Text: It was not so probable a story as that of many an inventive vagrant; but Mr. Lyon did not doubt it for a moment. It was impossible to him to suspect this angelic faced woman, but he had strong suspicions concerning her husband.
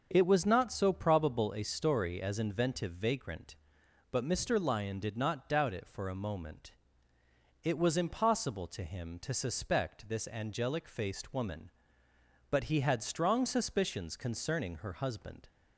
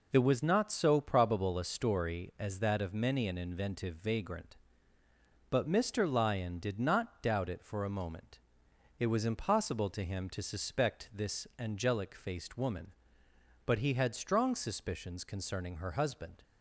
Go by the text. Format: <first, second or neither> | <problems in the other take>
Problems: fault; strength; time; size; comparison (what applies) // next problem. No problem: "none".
second | starts louder than the rest; until 1.1 s; 6.5 dB // skips "that of many an"; at 2.3 s